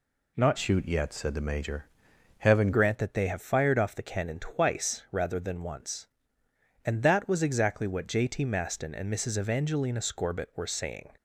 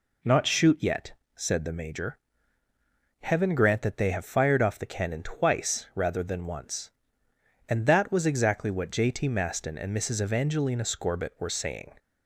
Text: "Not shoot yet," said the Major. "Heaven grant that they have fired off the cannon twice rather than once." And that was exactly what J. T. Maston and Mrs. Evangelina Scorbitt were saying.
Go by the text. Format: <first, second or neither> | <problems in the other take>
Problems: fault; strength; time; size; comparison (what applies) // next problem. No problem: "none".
second | changes voice from "shoot" to "Heaven"; from 0.5 to 2.7 s; 2.2 s long